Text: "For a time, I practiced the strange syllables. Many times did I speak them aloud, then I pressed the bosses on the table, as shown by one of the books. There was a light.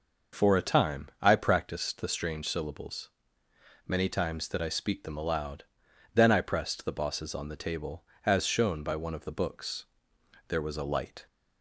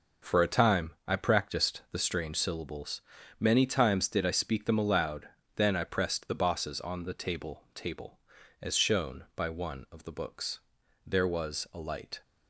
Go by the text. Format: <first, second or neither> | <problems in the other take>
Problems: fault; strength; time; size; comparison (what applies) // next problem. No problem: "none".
first | says "table" twice; at 7.7 s